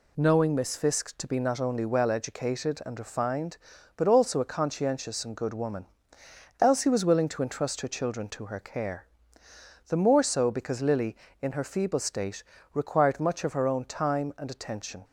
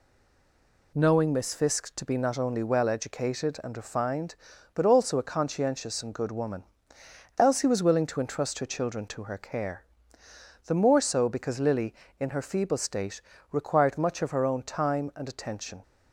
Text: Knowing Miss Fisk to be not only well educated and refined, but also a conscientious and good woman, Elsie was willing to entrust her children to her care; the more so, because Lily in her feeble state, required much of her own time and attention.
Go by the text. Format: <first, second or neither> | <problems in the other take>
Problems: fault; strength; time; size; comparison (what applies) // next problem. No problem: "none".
first | stays silent before the first word; slight; until 0.9 s; 0.9 s long